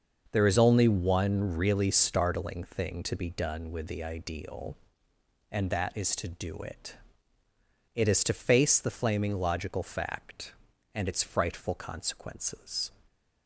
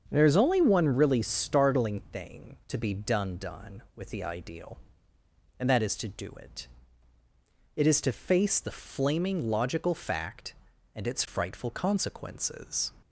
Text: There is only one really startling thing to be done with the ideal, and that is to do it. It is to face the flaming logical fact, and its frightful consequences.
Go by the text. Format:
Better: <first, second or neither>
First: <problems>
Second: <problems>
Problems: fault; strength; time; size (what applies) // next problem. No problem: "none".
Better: first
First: starts louder than the rest; noticeable; until 1.3 s; 6 dB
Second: starts louder than the rest; until 1.1 s; 7 dB // says "done" twice; at 3.3 s